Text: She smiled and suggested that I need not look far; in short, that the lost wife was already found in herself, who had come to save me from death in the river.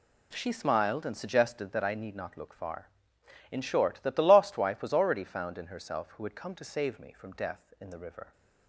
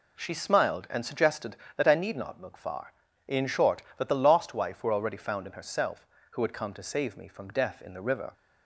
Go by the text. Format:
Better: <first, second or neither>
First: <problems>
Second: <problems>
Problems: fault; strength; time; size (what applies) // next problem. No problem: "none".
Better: first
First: none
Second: says "were" for "was"; at 4.8 s